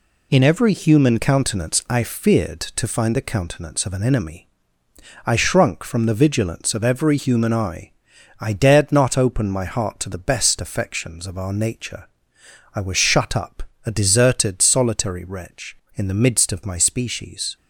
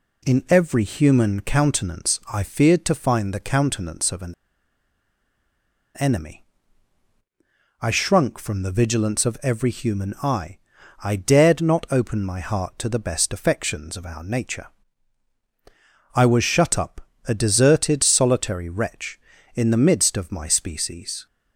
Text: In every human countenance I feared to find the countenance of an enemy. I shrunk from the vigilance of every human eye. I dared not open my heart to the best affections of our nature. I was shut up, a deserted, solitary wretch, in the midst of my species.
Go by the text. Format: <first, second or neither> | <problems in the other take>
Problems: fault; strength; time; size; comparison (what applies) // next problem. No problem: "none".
first | pauses between "an" and "enemy"; strong; at 4.3 s; 1.6 s long